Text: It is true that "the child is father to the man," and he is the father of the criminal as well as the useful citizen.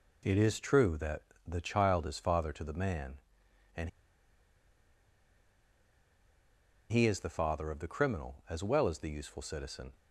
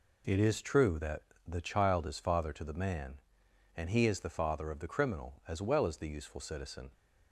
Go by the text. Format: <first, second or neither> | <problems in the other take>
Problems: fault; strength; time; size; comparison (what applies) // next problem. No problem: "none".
second | pauses between "that" and "the"; slight; at 1.1 s; 0.26 s long; slight in the second // pauses between "and" and "he"; strong; at 3.8 s; 3.0 s long